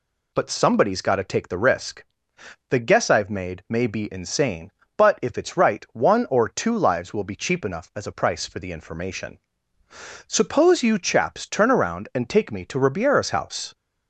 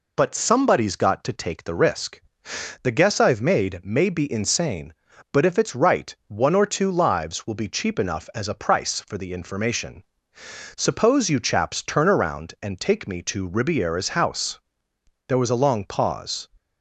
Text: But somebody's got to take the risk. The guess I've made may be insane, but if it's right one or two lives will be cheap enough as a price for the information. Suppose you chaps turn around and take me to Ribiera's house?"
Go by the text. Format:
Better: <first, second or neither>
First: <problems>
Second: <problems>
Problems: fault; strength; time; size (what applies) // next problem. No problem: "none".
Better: first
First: none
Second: goes on to say "There was a long pause"; noticeable; from 15.2 s on; 1.2 s long